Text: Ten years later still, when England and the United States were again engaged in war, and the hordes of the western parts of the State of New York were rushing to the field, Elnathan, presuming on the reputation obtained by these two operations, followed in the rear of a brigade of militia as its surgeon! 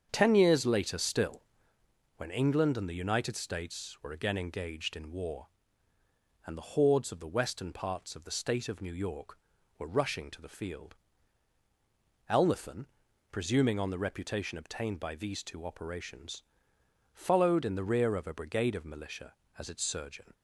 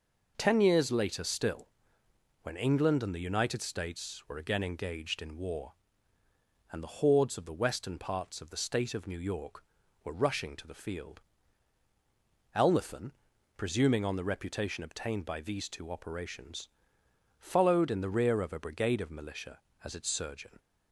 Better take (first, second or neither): second